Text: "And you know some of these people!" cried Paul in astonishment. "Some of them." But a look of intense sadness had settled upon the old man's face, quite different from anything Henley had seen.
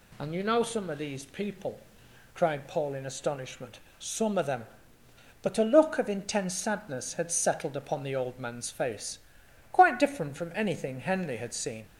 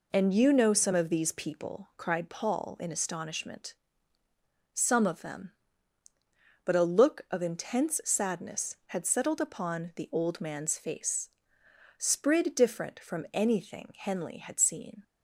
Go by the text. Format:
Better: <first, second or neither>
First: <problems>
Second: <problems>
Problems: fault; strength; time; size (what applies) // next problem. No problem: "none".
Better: first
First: none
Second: says "sprid" for "quite"; at 11.9 s